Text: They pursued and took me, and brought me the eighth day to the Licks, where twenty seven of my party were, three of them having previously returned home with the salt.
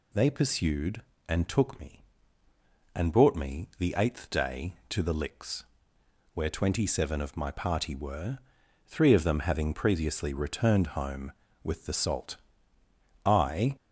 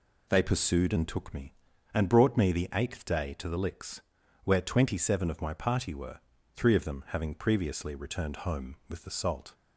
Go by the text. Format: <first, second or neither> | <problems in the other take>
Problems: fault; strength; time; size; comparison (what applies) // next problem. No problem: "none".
second | goes on to say "I"; from 13.2 s on; 0.52 s long